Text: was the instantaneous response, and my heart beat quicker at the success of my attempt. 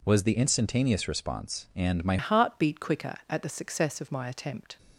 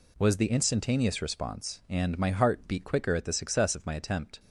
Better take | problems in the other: second | changes voice at "heart"; from 2.1 s on; 2.6 s long

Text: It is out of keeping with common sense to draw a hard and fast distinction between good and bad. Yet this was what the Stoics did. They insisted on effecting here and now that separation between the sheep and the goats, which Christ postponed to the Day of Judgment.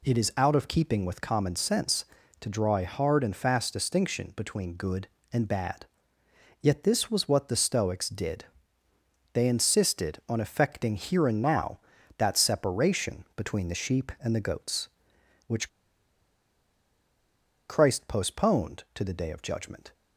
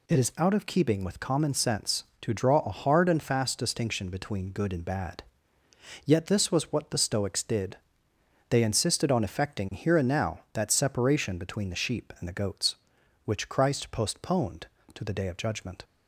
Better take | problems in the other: second | pauses between "which" and "Christ"; strong; at 15.6 s; 1.9 s long

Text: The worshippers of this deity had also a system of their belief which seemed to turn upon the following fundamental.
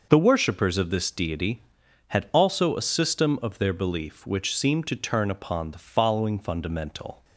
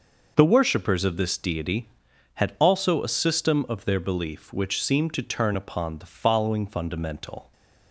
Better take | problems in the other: neither | none

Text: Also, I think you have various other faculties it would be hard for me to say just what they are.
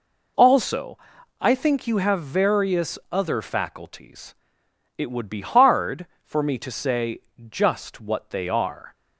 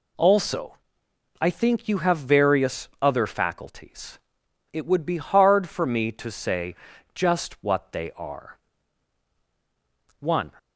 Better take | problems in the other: first | pauses between "faculties" and "it"; noticeable; at 4.1 s; 0.54 s long; noticeable in the first // pauses between "say" and "just"; at 6.7 s; 0.39 s long; slight in the first // goes on to say "One"; slight; from 10.1 s on; 0.34 s long

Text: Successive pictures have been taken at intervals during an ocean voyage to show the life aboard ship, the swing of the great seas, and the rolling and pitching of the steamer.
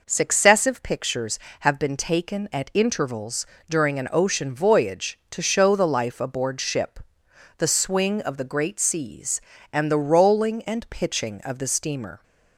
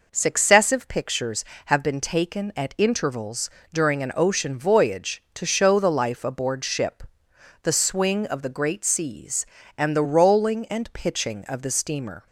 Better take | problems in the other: neither | pauses between "intervals" and "during"; slight; the same in both

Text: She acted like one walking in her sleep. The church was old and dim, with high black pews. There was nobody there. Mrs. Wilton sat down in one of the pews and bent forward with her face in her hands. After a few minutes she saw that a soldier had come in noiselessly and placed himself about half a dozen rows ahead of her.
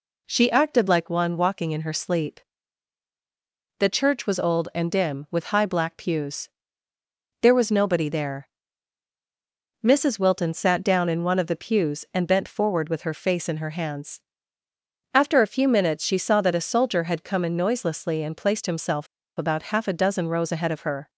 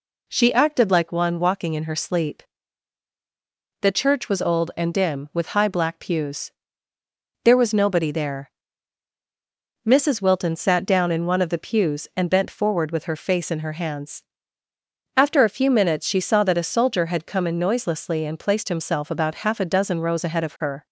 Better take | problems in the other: second | pauses between "himself" and "about"; slight; at 19.0 s; 0.31 s long

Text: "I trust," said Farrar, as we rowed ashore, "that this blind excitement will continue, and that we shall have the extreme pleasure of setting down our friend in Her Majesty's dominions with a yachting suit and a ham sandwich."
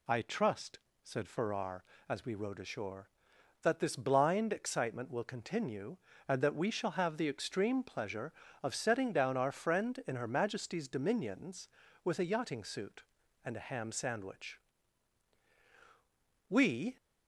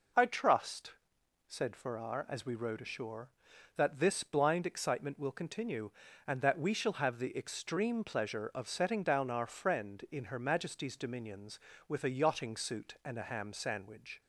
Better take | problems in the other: second | goes on to say "We"; slight; from 16.4 s on; 0.48 s long

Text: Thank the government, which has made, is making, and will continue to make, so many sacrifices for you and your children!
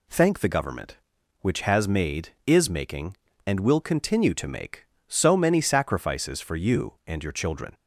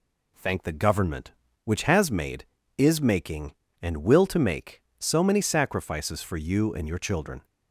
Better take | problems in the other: first | skips "continue"; at 4.2 s

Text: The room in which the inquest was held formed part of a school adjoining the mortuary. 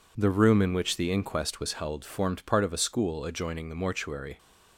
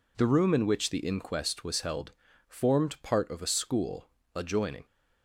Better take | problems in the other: first | pauses between "held" and "formed"; slight; at 2.1 s; 0.34 s long // pauses between "school" and "adjoining"; slight; at 4.0 s; 0.26 s long // stops before "the mortuary"; at 4.8 s

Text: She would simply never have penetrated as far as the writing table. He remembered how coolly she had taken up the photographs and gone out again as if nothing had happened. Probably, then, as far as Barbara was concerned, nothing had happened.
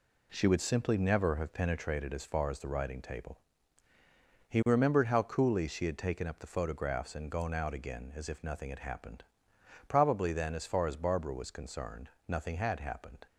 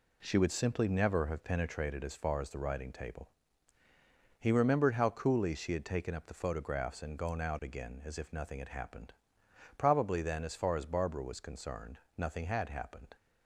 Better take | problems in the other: neither | none

